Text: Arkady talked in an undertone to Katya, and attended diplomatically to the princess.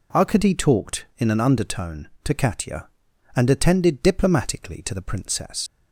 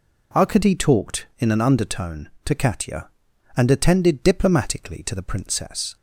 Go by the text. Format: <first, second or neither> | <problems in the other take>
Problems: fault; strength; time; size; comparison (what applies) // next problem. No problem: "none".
second | leaves "princess" unfinished; at 5.6 s; 90 ms